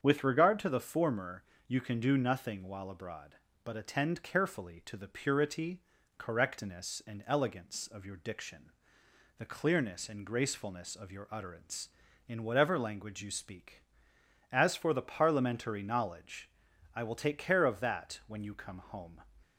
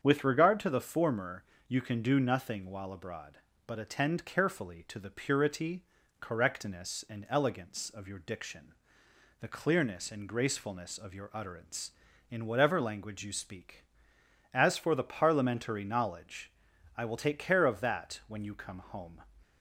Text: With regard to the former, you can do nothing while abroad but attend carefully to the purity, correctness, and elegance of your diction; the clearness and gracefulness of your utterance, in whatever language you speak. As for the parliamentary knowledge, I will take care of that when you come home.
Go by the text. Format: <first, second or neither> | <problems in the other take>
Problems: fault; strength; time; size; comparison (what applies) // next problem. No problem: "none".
neither | starts louder than the rest; strong; the same in both